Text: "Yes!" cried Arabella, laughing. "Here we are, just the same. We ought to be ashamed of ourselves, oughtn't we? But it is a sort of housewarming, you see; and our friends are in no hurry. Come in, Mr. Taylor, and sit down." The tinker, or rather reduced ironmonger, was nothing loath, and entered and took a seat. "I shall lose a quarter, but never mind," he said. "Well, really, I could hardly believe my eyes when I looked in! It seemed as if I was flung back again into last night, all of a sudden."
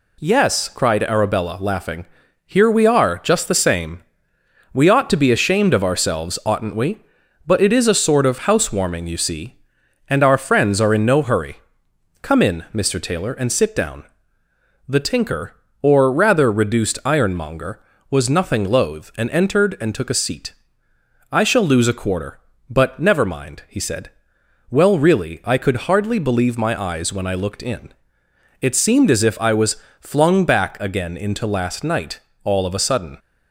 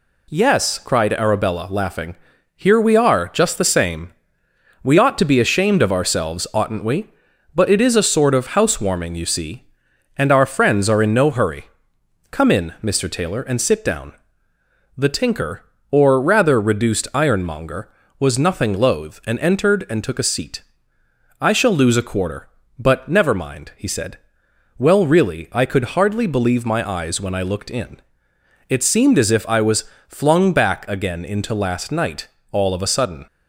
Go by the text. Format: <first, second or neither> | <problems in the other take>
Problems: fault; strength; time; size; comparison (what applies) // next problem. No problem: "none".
neither | pauses between "was" and "flung"; slight; the same in both